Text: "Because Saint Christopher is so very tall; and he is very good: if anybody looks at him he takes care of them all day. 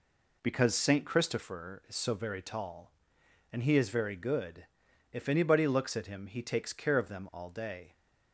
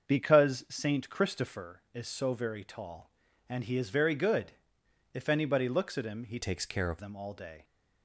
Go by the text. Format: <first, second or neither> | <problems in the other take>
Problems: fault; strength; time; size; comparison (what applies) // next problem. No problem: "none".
first | starts louder than the rest; until 1.1 s; 6.5 dB // changes voice from "takes" to "of"; from 6.4 to 7.0 s; 0.6 s long